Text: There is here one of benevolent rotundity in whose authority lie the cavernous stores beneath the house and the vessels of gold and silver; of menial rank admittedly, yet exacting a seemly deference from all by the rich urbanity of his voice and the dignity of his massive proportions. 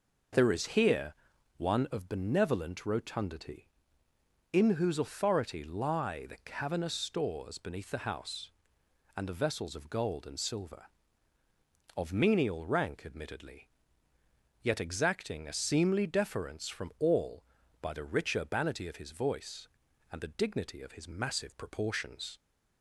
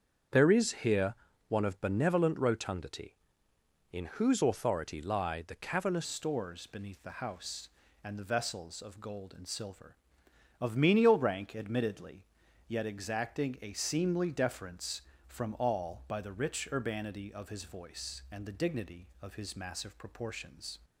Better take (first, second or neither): first